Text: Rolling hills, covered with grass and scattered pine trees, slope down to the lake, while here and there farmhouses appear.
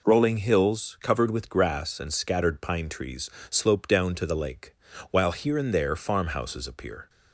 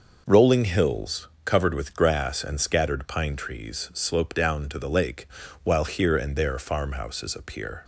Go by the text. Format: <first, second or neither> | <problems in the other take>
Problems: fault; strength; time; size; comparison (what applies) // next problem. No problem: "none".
neither | none